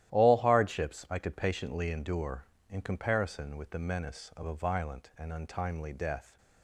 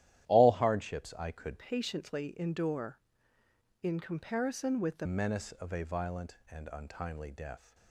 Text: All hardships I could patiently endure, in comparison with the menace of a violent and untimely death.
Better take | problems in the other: first | starts louder than the rest; strong; until 1.3 s; 12.5 dB; strong in the first // changes voice from "patiently" to "the"; from 1.5 to 5.0 s; 3.5 s long

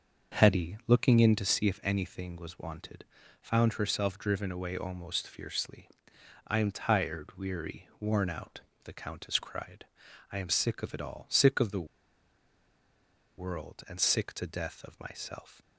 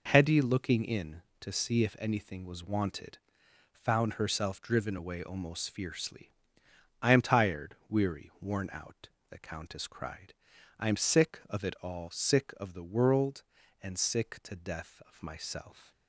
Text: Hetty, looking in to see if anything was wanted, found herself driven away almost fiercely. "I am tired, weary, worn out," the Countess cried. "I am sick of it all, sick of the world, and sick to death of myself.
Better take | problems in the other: second | starts louder than the rest; until 1.4 s; 6 dB // pauses between "the" and "world"; strong; at 11.8 s; 1.5 s long

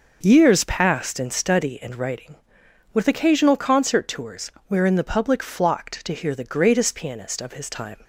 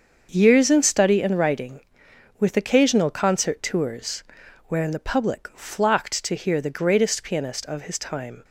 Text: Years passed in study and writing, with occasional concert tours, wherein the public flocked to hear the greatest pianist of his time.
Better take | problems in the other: first | starts louder than the rest; until 1.3 s; 6.5 dB // skips "passed"; at 0.6 s

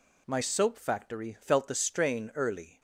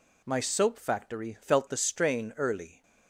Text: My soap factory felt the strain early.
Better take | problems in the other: neither | none

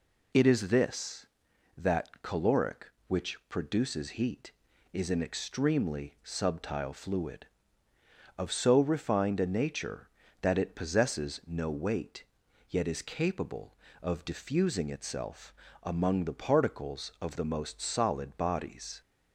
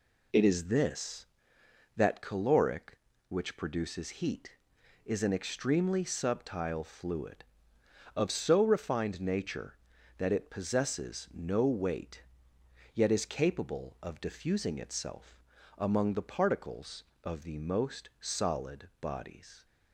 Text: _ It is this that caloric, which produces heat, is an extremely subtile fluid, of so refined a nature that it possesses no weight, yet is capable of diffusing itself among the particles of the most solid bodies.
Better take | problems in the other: first | skips "a"; at 9.1 s // pauses between "itself" and "among"; slight; at 15.4 s; 0.36 s long; slight in the first

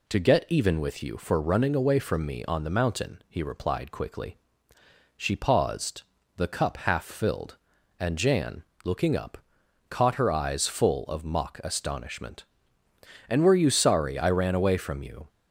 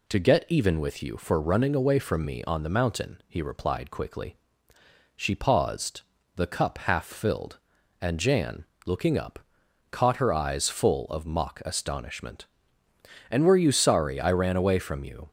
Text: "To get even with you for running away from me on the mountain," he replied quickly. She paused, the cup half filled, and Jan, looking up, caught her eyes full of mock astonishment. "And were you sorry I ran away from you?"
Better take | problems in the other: neither | none

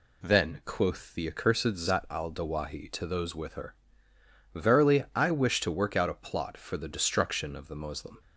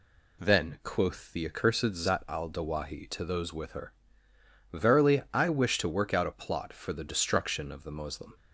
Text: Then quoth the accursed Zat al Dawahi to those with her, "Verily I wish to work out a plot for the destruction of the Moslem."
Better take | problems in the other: neither | none

